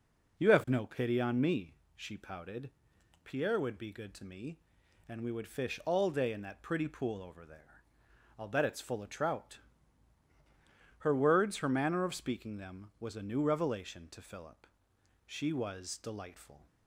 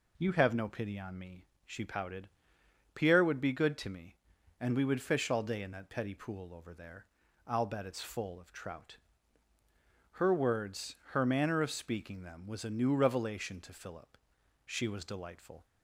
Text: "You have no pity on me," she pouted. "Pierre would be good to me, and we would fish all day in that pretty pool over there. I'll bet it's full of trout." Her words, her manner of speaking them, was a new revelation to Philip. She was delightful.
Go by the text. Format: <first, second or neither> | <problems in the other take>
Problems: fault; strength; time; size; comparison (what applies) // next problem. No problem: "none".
first | says "petty" for "pretty"; at 5.8 s